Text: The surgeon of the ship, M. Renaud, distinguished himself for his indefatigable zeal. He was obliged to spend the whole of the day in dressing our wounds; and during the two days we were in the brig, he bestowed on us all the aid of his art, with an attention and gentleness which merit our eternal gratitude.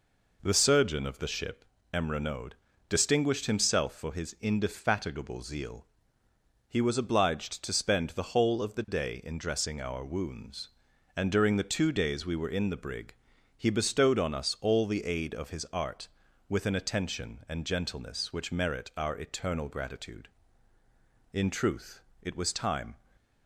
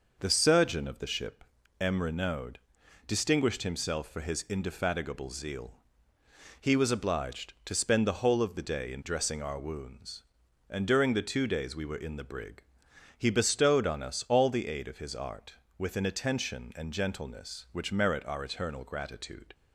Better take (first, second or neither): second